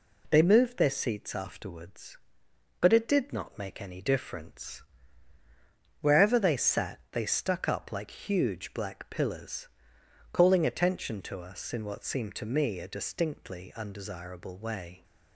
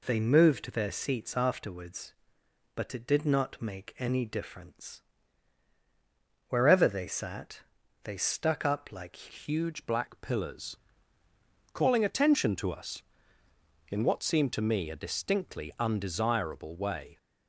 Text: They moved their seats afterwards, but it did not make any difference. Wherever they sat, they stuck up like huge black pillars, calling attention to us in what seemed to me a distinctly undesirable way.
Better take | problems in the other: first | changes voice at "huge"; from 9.3 s on; 7.8 s long

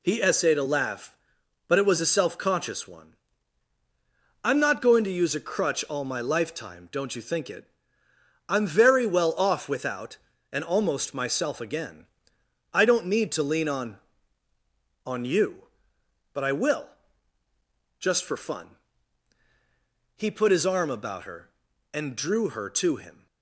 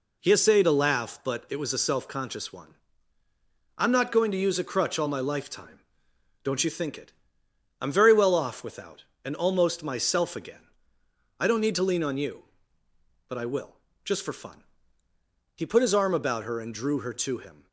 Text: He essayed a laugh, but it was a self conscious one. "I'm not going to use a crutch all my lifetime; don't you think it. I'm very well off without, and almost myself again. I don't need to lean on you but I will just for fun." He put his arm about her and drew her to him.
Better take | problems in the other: second | says "on" twice; at 15.0 s // pauses between "will" and "just"; at 16.8 s; 1.1 s long; slight in the second

